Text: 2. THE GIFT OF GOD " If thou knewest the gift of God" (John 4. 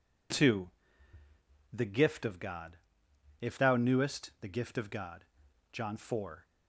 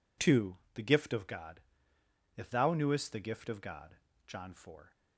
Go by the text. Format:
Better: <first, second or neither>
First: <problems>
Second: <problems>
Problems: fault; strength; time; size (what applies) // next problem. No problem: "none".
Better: neither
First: none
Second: none